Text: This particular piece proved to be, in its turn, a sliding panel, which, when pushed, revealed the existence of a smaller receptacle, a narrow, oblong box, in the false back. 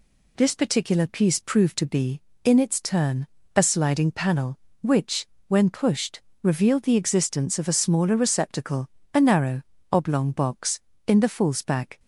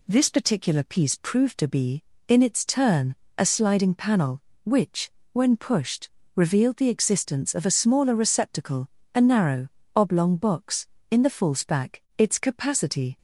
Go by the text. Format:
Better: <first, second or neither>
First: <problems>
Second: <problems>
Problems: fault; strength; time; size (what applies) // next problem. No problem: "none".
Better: first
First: none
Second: goes on to say "Its capacity"; noticeable; from 12.1 s on; 1.0 s long